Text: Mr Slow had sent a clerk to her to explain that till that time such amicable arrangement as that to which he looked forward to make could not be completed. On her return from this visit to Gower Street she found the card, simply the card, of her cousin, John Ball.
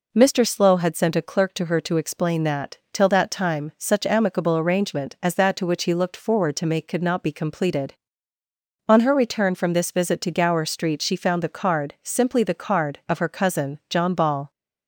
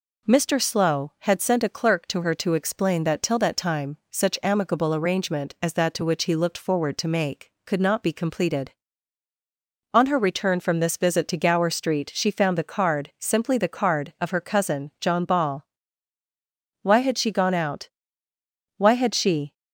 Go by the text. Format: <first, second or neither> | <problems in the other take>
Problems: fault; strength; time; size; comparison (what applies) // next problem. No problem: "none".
first | goes on to say "Why had she gone out Why had she"; strong; from 16.8 s on; 2.7 s long